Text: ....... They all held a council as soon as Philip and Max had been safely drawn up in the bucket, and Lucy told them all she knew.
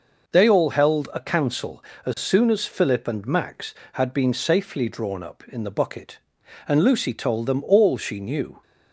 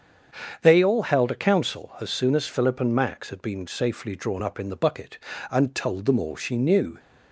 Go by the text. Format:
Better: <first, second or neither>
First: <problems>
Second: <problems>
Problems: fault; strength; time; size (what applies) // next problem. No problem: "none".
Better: first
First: none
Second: starts louder than the rest; until 1.4 s; 7 dB // skips "Lucy"; at 5.7 s